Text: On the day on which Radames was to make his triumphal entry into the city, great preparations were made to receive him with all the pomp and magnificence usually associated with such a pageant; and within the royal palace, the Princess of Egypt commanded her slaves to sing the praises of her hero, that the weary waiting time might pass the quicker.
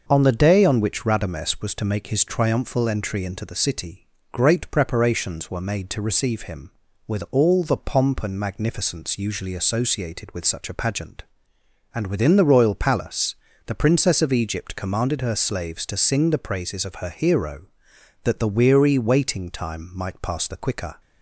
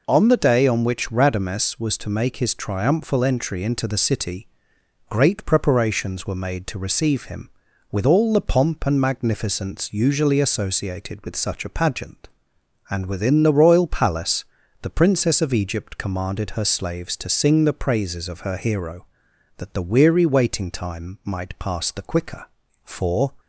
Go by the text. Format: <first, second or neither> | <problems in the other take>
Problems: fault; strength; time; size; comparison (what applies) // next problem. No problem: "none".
first | goes on to say "For"; from 22.8 s on; 0.50 s long